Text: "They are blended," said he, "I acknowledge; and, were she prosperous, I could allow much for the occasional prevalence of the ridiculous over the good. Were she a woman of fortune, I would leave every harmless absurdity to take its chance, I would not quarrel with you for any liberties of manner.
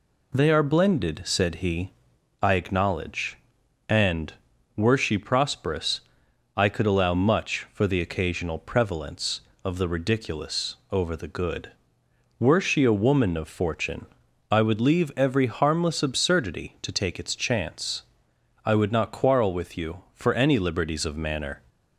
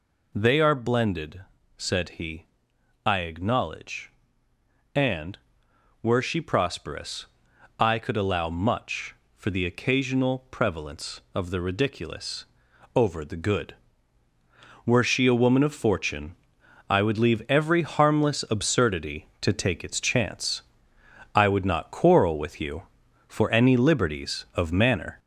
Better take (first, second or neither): first